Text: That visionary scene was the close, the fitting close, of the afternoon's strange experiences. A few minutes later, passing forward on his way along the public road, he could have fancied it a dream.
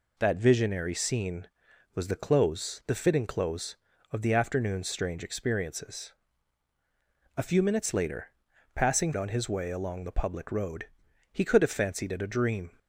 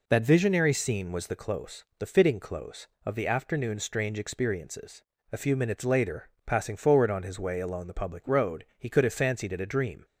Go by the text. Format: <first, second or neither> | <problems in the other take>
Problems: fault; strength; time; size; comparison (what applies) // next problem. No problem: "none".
second | skips "forward"; at 9.1 s